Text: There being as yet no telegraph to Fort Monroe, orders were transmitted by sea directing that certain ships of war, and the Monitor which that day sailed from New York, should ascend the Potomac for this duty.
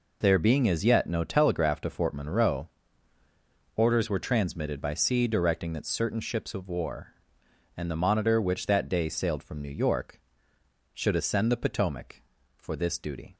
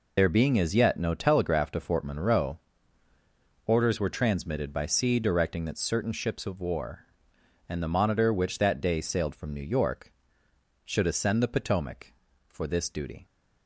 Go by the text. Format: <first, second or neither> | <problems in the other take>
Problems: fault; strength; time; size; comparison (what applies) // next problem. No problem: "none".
first | loses the start of "There"; at 0.1 s; 65 ms